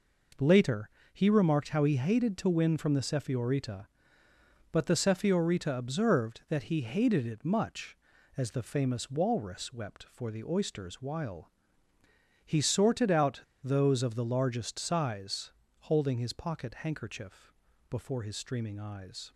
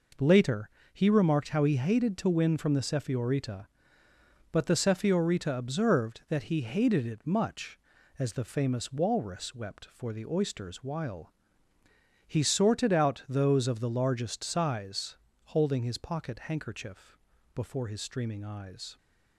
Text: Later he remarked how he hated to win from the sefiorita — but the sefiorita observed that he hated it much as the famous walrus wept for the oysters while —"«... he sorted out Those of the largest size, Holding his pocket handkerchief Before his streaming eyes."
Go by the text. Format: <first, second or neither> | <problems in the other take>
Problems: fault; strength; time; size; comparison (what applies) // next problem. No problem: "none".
second | pauses between "Later" and "he"; slight; at 0.8 s; 0.24 s long; slight in the second // pauses between "out" and "Those"; slight; at 13.4 s; 0.21 s long // pauses between "handkerchief" and "Before"; slight; at 17.5 s; 0.36 s long; slight in the second